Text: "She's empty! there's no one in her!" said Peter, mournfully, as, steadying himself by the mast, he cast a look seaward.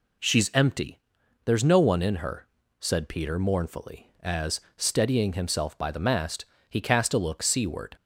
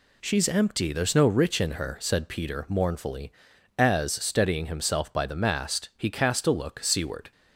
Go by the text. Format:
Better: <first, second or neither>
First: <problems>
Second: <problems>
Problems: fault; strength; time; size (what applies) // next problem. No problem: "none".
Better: first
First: none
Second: says "rich" for "one"; at 1.2 s